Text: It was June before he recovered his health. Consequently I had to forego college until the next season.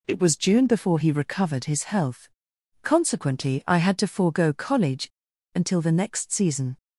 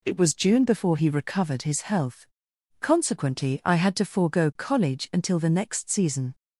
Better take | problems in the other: second | pauses between "college" and "until"; noticeable; at 5.0 s; 0.46 s long

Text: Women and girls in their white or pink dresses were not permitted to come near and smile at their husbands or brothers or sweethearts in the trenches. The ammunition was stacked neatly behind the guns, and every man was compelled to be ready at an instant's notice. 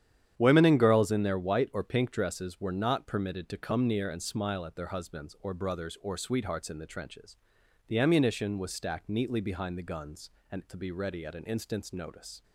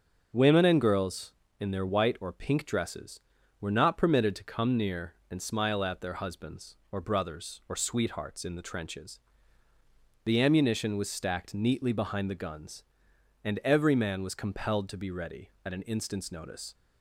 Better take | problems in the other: second | starts louder than the rest; strong; until 1.3 s; 9.5 dB; also in the second // skips "every man was compelled"; at 10.6 s

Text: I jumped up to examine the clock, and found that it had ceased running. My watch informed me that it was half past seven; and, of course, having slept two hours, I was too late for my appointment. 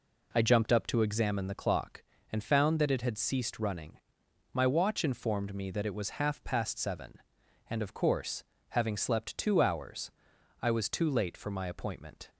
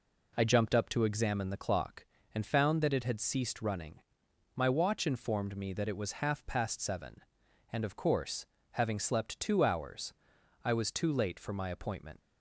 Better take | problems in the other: first | leaves "appointment" unfinished; at 12.2 s; 115 ms

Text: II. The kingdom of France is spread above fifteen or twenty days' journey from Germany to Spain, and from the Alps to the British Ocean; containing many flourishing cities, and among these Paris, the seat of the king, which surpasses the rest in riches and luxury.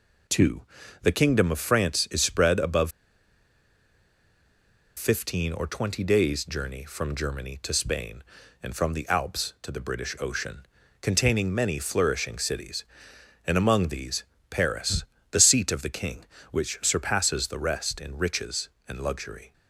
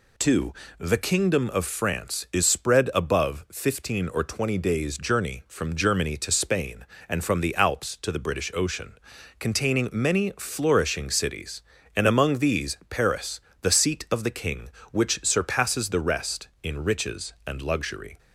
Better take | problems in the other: second | pauses between "above" and "fifteen"; strong; at 2.9 s; 2.0 s long // pauses between "these" and "Paris"; slight; at 14.2 s; 0.26 s long

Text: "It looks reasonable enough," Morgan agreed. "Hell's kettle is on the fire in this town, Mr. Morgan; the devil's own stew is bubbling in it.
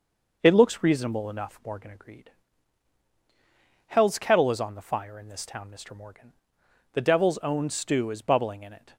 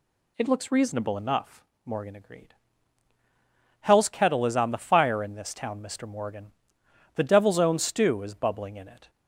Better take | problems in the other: neither | none

